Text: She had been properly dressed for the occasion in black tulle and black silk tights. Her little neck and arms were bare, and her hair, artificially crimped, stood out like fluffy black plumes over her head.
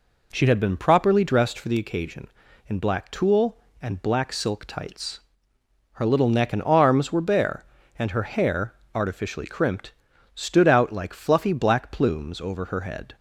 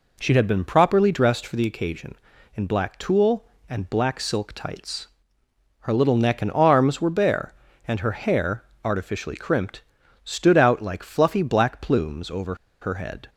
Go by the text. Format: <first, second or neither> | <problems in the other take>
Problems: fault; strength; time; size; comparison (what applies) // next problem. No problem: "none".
first | pauses between "over" and "her"; slight; at 12.5 s; 0.26 s long